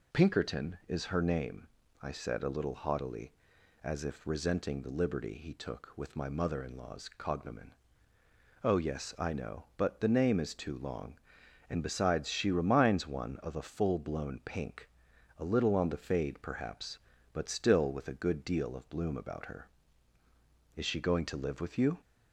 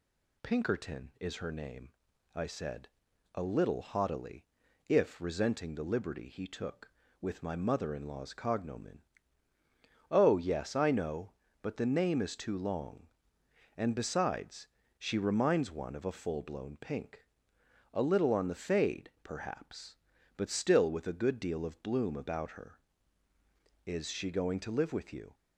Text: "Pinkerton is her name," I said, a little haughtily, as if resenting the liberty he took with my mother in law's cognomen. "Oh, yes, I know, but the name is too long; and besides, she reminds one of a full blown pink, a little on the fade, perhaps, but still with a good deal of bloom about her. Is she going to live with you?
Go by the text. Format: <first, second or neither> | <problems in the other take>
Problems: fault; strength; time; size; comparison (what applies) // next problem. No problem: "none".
first | skips "as"; at 4.6 s